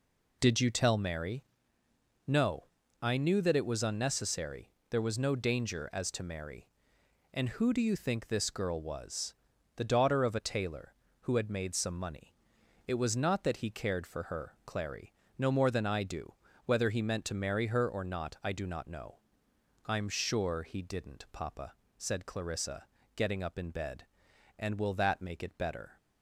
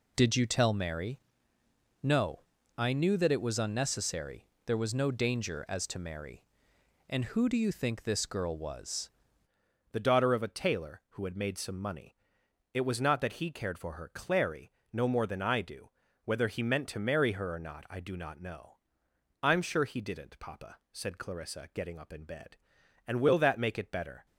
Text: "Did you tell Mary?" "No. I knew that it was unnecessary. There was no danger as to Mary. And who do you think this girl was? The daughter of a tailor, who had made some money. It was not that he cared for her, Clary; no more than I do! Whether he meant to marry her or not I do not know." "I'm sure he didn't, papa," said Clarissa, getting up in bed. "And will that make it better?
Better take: first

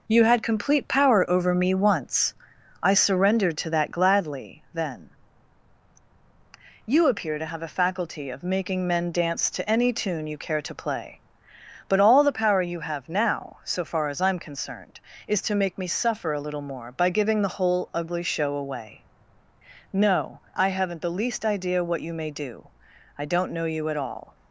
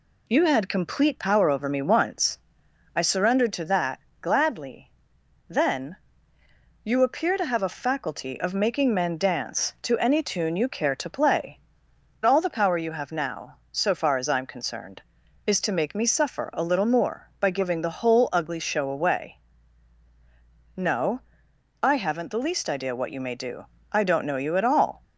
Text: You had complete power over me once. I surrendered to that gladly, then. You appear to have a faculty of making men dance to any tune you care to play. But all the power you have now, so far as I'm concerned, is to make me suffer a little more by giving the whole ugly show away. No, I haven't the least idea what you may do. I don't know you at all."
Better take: first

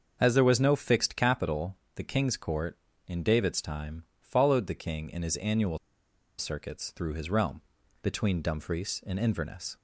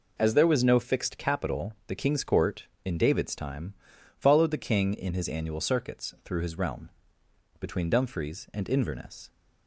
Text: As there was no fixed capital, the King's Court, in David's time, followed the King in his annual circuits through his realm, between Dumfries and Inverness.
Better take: second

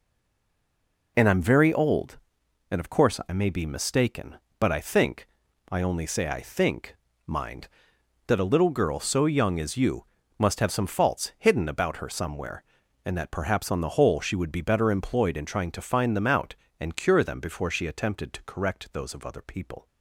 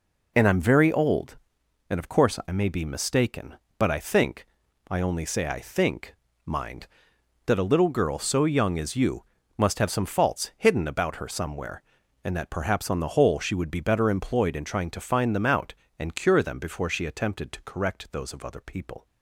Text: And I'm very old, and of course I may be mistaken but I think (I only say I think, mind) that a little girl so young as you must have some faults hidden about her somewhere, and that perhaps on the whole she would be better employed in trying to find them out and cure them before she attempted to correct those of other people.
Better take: second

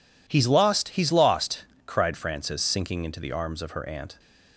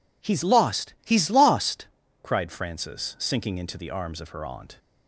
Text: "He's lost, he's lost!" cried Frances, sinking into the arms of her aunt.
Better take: neither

